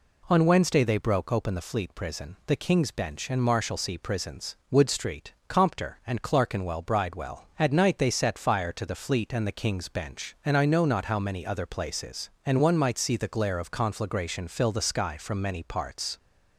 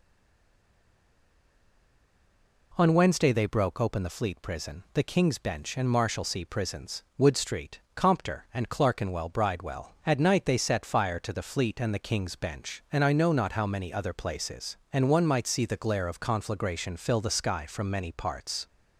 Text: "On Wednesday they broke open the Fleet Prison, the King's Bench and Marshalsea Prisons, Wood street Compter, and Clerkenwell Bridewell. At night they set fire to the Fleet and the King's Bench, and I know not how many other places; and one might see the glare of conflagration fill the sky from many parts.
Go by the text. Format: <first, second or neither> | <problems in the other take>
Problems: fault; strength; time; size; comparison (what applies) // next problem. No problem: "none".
first | stays silent before the first word; strong; until 2.7 s; 2.7 s long // pauses between "street" and "Compter"; slight; at 7.8 s; 0.16 s long; slight in the first